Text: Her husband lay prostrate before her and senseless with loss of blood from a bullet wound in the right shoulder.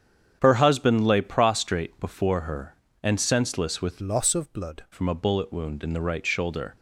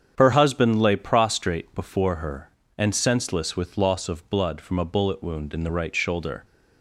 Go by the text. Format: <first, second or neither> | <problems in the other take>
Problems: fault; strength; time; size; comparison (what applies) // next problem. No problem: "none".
second | starts louder than the rest; strong; until 1.4 s; 8.5 dB; strong in the second // changes voice from "loss" to "blood"; from 3.9 to 4.8 s; 0.9 s long